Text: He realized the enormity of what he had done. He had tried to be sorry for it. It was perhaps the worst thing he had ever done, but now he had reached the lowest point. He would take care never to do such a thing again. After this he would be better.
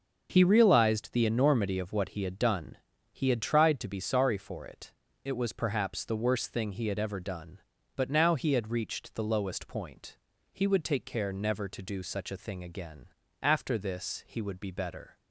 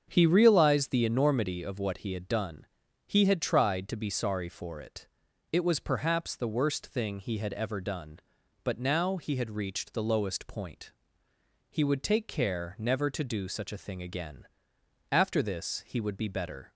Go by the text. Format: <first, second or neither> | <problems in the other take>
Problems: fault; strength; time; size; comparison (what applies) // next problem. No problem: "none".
neither | starts louder than the rest; the same in both